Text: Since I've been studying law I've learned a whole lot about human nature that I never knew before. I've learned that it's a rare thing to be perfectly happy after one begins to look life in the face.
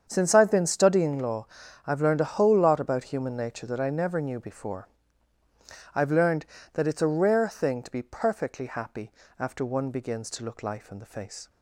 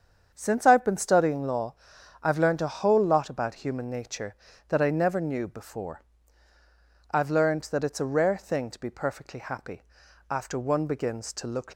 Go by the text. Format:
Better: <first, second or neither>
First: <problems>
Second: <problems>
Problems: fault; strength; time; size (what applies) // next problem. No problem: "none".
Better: first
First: starts louder than the rest; strong; until 1.0 s; 7.5 dB // pauses between "law" and "I've"; at 1.4 s; 0.38 s long // pauses between "happy" and "after"; slight; at 9.1 s; 0.26 s long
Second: starts louder than the rest; strong; until 1.3 s; 7.5 dB // pauses between "law" and "I've"; noticeable; at 1.7 s; 0.48 s long // pauses between "happy" and "after"; noticeable; at 9.8 s; 0.46 s long // stops before "life in the face"; at 11.7 s